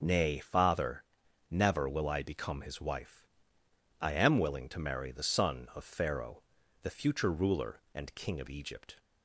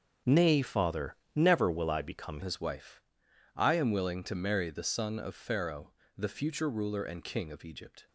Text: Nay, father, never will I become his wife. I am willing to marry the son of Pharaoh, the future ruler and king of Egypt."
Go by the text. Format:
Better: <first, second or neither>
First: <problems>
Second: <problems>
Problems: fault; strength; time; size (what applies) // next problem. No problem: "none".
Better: first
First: none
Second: starts louder than the rest; until 1.4 s; 6.5 dB // changes voice at "his"; from 2.4 s on; 5.6 s long